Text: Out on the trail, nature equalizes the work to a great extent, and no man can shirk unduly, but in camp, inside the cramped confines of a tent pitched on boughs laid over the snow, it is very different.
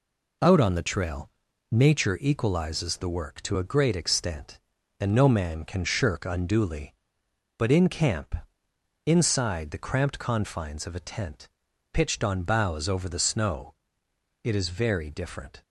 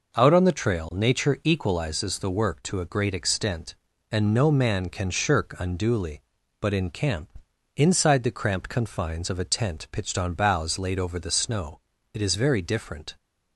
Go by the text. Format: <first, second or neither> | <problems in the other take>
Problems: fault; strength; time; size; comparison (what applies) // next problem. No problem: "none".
second | pauses between "tent" and "pitched"; noticeable; at 11.4 s; 0.46 s long // skips "laid"; at 12.8 s